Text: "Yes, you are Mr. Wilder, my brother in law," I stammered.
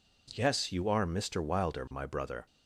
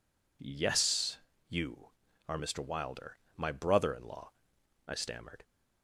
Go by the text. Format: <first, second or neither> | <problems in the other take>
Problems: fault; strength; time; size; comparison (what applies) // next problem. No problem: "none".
second | stops before "in law I stammered"; at 2.4 s